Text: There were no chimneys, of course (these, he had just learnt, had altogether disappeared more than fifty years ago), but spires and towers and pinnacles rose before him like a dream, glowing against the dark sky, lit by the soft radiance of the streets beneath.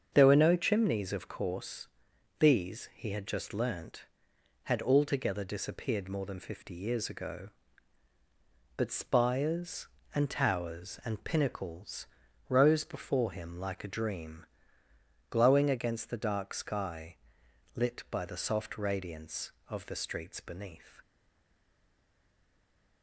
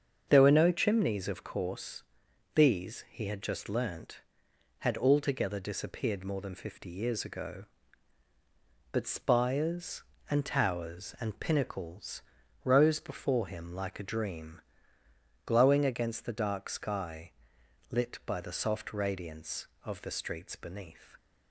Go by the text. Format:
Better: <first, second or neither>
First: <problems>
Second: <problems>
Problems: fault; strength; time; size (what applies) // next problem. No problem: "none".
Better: second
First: starts louder than the rest; until 1.1 s; 7 dB // pauses between "pinnacles" and "rose"; at 12.0 s; 0.42 s long // stays silent after the last word; noticeable; from 21.0 s on; 2.0 s long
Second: starts louder than the rest; until 1.2 s; 7 dB // pauses between "pinnacles" and "rose"; at 12.2 s; 0.42 s long